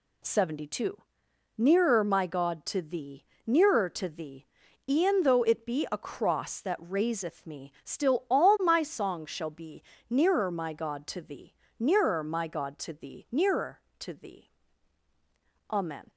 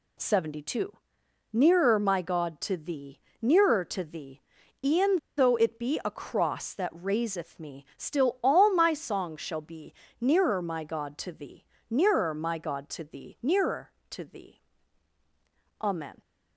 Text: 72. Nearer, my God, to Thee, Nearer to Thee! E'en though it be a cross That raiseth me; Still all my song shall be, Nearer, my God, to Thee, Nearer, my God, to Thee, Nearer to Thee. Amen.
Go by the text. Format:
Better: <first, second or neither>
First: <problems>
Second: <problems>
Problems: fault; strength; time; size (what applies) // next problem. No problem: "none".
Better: first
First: none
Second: pauses between "E'en" and "though"; slight; at 5.1 s; 0.18 s long